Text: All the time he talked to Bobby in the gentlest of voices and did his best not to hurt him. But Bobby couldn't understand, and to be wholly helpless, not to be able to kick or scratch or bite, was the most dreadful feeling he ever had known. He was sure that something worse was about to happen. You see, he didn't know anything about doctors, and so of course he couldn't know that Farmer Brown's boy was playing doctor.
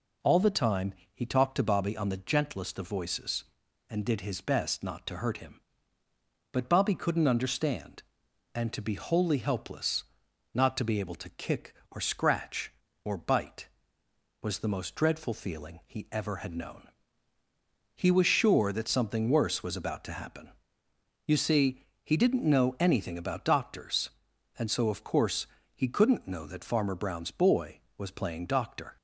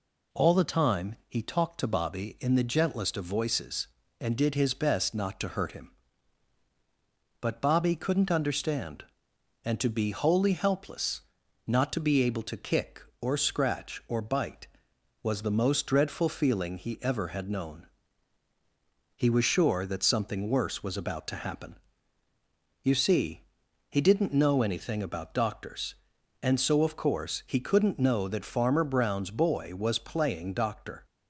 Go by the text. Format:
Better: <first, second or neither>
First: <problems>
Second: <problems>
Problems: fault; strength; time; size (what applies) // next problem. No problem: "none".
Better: second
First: pauses between "time" and "he"; slight; at 0.9 s; 0.20 s long // says "on" for "in"; at 1.9 s // pauses between "course" and "he"; slight; at 25.4 s; 0.28 s long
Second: none